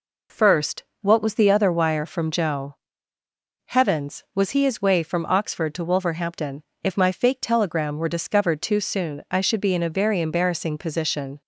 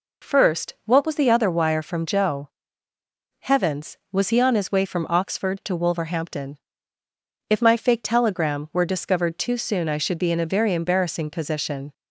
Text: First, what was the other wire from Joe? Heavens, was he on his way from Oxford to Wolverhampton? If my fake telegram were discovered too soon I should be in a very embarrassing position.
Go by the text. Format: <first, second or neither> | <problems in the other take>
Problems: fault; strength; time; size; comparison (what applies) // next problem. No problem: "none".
second | skips "on"; at 4.6 s